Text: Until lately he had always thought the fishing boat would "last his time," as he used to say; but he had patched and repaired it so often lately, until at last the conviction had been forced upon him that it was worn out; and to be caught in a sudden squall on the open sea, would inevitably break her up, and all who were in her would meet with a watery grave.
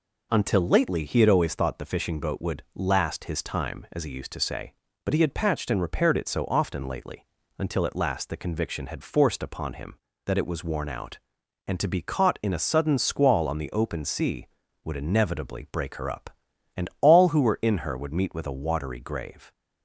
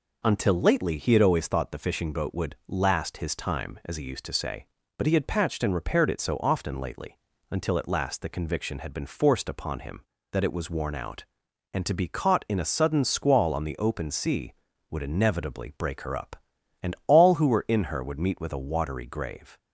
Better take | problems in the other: second | skips "been"; at 9.0 s

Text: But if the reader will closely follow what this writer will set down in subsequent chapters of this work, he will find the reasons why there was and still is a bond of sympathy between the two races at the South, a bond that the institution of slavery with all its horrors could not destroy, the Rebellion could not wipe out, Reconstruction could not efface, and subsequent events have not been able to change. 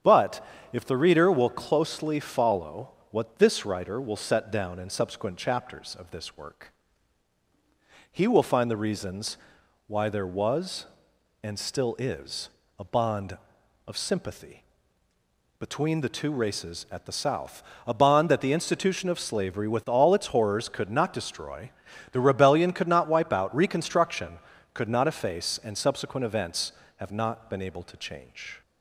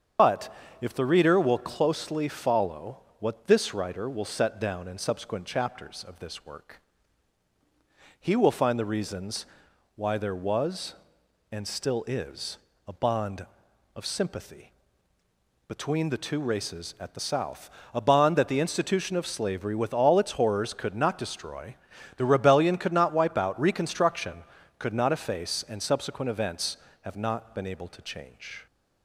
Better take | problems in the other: first | loses the start of "But"; at 0.1 s; 80 ms // starts louder than the rest; strong; until 1.4 s; 7 dB; strong in the first // pauses between "But" and "if"; slight; at 0.5 s; 0.28 s long; slight in the first // pauses between "follow" and "what"; slight; at 2.9 s; 0.22 s long; slight in the first // pauses between "reasons" and "why"; noticeable; at 9.4 s; 0.50 s long; noticeable in the first // pauses between "is" and "a"; slight; at 12.5 s; 0.30 s long; slight in the first // pauses between "sympathy" and "between"; noticeable; at 14.7 s; 0.96 s long; noticeable in the first

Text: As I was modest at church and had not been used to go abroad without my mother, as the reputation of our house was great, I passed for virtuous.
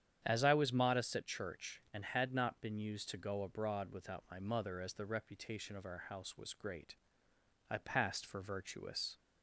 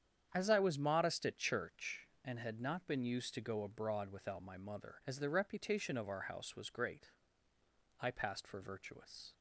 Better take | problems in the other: neither | starts louder than the rest; strong; the same in both

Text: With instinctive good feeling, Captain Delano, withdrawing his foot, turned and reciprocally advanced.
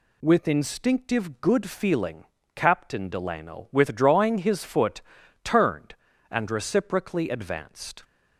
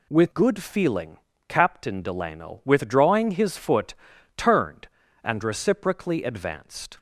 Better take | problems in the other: first | skips "instinctive"; at 0.3 s

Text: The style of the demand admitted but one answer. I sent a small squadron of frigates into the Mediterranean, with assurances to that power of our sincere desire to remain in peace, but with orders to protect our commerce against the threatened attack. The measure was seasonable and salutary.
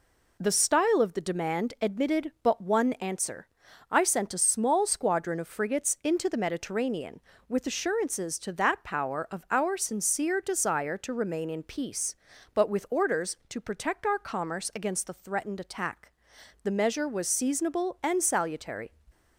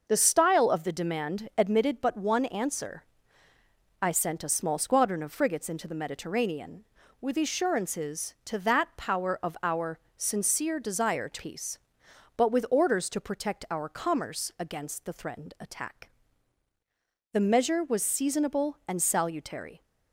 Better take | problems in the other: first | pauses between "our" and "sincere"; slight; at 9.9 s; 0.18 s long // skips "remain in"; at 11.3 s

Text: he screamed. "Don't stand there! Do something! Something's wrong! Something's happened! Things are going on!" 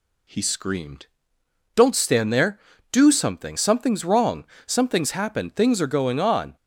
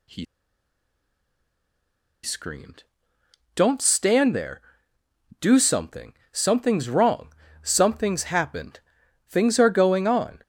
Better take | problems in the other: first | pauses between "he" and "screamed"; strong; at 0.2 s; 1.9 s long

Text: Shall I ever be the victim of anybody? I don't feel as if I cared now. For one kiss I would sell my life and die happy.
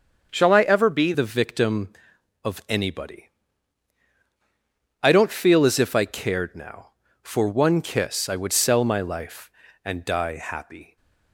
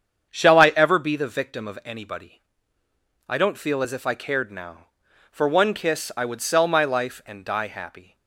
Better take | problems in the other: second | starts louder than the rest; until 1.3 s; 6.5 dB; strong in the second // changes voice at "the"; from 1.1 s on; 9.8 s long

